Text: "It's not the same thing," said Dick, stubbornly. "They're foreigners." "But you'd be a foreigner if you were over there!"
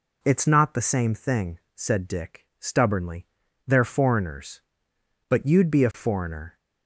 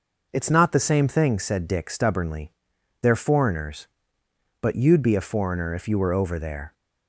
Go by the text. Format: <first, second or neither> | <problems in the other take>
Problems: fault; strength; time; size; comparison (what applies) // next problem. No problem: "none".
second | stops before "if you were over there"; at 6.5 s